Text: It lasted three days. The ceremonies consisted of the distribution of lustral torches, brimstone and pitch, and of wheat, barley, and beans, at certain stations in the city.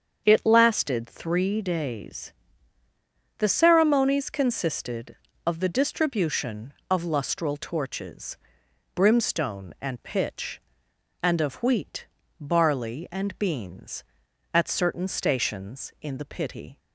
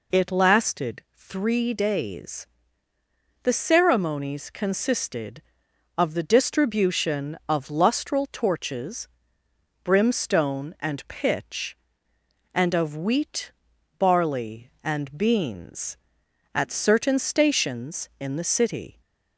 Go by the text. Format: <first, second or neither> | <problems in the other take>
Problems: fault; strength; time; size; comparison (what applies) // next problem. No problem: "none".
second | starts louder than the rest; strong; until 1.2 s; 7 dB // says "pity" for "city"; at 16.2 s